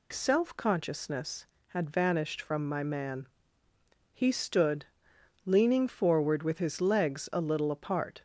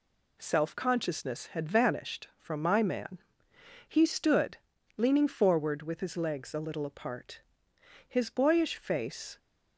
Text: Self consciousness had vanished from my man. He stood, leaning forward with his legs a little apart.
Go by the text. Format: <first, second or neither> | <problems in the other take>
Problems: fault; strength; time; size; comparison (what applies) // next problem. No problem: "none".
first | goes on to say "His boyish face"; noticeable; from 8.0 s on; 1.3 s long